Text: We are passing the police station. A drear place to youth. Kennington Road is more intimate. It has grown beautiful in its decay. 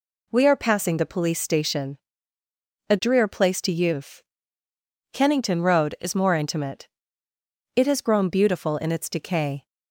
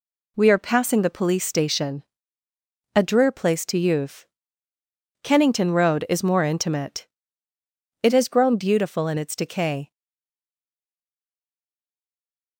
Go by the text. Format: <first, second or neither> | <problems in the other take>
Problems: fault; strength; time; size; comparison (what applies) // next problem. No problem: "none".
first | stays silent after the last word; strong; from 9.9 s on; 2.6 s long